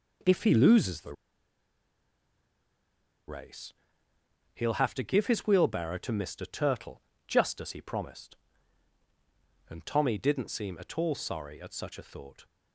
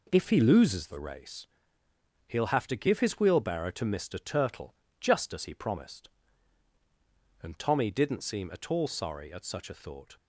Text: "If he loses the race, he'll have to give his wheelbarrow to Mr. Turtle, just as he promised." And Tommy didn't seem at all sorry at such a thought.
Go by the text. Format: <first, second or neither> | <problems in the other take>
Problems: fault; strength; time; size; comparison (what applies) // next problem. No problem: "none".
second | pauses between "the" and "race"; strong; at 1.1 s; 2.1 s long